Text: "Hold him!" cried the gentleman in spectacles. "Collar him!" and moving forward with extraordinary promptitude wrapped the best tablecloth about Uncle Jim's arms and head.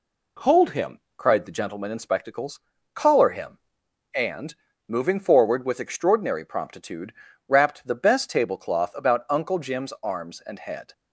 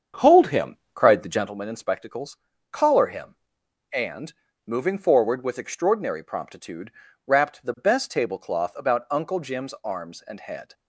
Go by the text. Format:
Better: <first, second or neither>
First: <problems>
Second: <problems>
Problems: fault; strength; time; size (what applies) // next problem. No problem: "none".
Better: first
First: pauses between "and" and "moving"; slight; at 4.5 s; 0.32 s long // pauses between "promptitude" and "wrapped"; slight; at 7.1 s; 0.34 s long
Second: starts louder than the rest; strong; until 1.5 s; 7.5 dB // pauses between "and" and "moving"; slight; at 4.3 s; 0.32 s long // pauses between "promptitude" and "wrapped"; slight; at 6.9 s; 0.34 s long